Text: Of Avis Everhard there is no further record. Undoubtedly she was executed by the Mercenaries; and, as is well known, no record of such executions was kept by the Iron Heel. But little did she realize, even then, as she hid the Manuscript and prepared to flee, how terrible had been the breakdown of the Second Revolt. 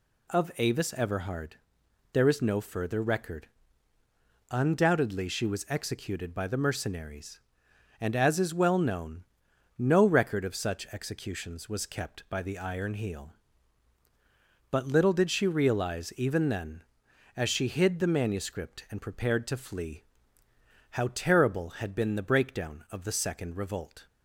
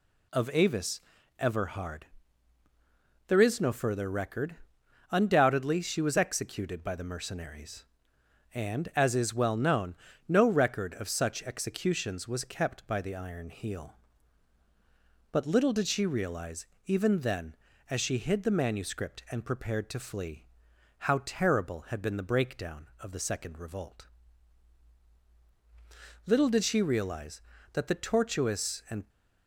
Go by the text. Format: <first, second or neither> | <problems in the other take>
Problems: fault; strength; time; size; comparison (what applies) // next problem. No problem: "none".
first | pauses between "Avis" and "Everhard"; at 1.0 s; 0.38 s long // pauses between "Everhard" and "there"; at 2.0 s; 1.2 s long; noticeable in the first // goes on to say "Little did she realize that the tortuous and"; strong; from 26.2 s on; 2.8 s long